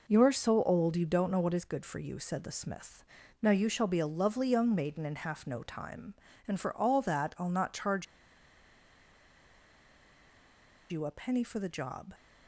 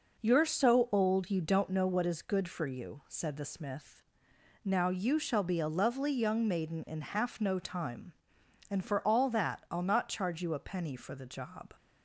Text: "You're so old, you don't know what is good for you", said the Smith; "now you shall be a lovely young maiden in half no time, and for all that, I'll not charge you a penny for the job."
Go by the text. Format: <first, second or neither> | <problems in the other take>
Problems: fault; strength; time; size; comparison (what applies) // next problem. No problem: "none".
second | pauses between "charge" and "you"; strong; at 8.0 s; 2.8 s long